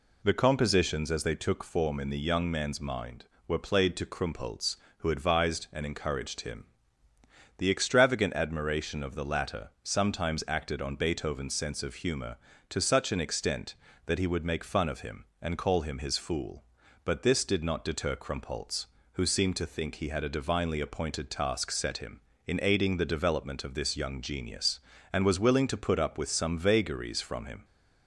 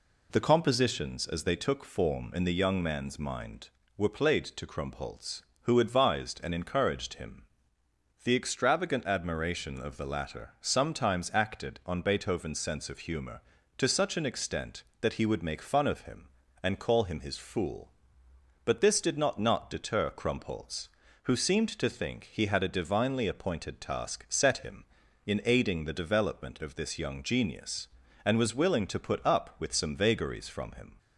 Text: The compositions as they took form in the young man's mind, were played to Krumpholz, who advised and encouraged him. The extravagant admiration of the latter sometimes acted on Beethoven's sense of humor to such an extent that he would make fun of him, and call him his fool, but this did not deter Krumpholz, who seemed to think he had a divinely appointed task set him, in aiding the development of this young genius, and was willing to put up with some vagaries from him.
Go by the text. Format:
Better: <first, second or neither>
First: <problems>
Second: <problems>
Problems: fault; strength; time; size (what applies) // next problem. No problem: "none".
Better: first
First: none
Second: says "not" twice; at 19.3 s